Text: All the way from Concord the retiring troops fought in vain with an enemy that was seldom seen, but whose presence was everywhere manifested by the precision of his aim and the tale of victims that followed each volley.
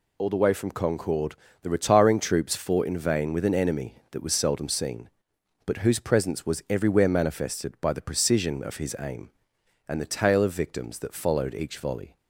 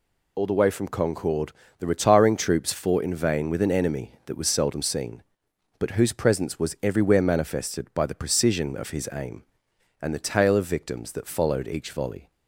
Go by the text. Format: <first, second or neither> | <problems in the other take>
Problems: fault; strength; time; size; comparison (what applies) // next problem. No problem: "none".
neither | pauses between "Concord" and "the"; slight; the same in both